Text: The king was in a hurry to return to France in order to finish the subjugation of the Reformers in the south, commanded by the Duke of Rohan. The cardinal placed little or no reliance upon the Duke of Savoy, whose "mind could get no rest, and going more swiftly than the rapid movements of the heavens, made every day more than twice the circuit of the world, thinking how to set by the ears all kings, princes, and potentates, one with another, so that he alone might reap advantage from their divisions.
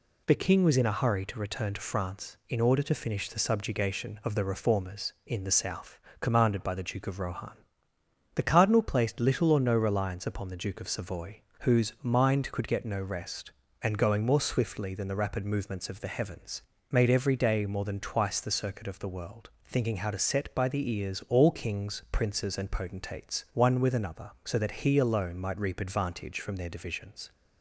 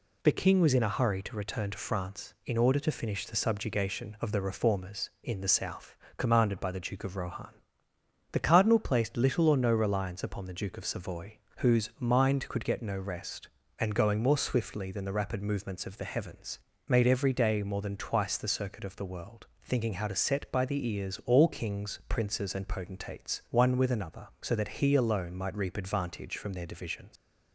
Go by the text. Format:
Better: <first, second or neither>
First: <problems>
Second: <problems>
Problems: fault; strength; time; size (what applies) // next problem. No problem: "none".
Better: first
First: none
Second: leaves "divisions" unfinished; at 27.1 s; 125 ms